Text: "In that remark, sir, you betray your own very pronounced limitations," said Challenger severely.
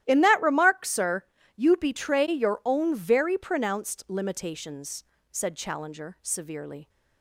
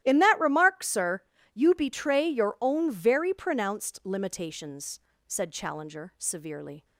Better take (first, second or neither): neither